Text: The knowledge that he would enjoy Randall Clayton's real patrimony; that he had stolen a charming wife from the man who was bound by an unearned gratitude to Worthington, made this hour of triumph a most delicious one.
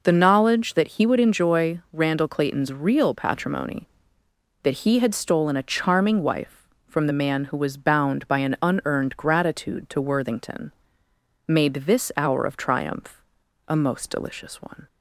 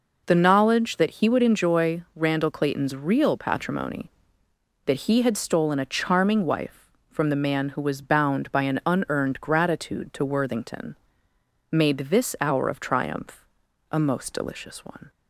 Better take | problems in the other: neither | pauses between "triumph" and "a"; noticeable; the same in both

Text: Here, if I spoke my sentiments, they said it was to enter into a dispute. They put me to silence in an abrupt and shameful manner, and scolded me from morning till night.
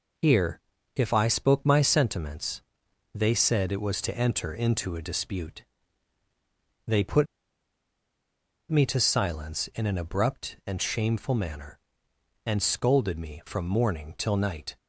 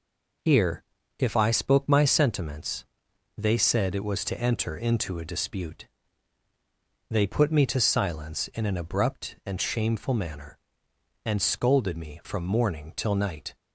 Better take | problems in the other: second | pauses between "put" and "me"; strong; at 7.2 s; 1.4 s long

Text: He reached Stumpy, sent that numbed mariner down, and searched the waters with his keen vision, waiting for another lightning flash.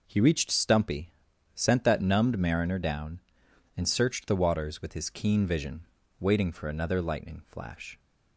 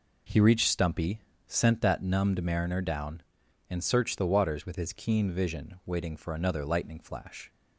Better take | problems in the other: neither | none

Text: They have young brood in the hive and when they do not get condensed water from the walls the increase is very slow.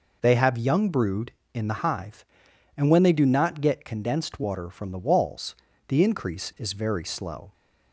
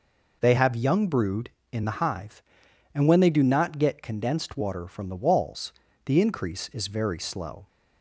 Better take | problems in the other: neither | pauses between "walls" and "the"; slight; the same in both

